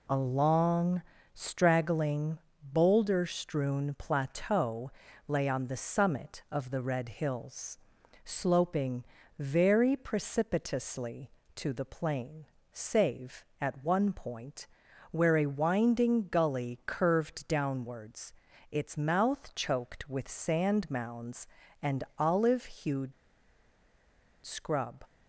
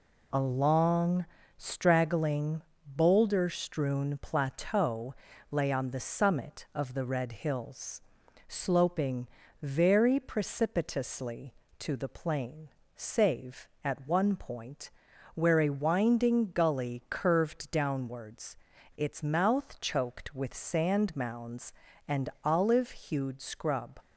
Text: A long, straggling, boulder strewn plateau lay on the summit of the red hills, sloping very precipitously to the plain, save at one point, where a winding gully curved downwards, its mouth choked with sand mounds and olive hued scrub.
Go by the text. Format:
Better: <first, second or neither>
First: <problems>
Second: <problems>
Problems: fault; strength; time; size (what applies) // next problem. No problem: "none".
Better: second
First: pauses between "plateau" and "lay"; slight; at 4.9 s; 0.36 s long // pauses between "sloping" and "very"; slight; at 9.0 s; 0.34 s long // pauses between "and" and "olive"; slight; at 22.0 s; 0.16 s long // pauses between "hued" and "scrub"; strong; at 23.1 s; 1.3 s long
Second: pauses between "plateau" and "lay"; slight; at 5.1 s; 0.36 s long // pauses between "sloping" and "very"; slight; at 9.2 s; 0.34 s long // pauses between "and" and "olive"; slight; at 22.2 s; 0.16 s long